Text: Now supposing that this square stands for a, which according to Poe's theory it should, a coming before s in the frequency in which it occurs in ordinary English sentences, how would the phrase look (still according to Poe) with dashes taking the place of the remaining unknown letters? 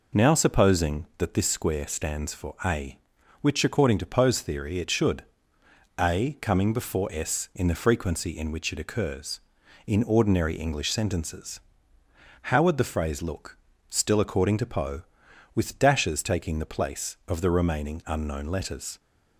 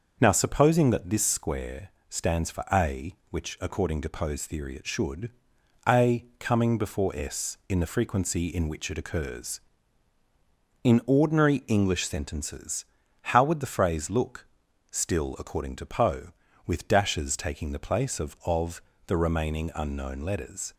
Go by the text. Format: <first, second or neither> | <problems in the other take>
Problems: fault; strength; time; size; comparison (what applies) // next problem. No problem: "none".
first | starts louder than the rest; until 1.2 s; 6.5 dB // pauses between "square" and "stands"; slight; at 1.8 s; 0.18 s long // pauses between "a" and "coming"; slight; at 6.2 s; 0.16 s long // says "of" twice; at 18.4 s